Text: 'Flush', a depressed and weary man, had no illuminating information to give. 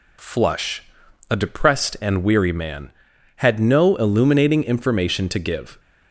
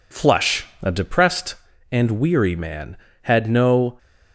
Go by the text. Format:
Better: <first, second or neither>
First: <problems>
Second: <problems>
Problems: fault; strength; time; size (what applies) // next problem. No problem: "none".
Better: first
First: none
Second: stops before "illuminating information to give"; at 3.9 s